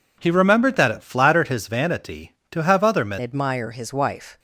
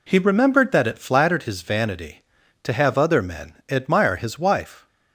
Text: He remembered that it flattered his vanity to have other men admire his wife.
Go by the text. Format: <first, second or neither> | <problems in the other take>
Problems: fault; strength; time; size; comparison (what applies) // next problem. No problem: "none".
second | changes voice at "admire"; from 3.1 s on; 1.2 s long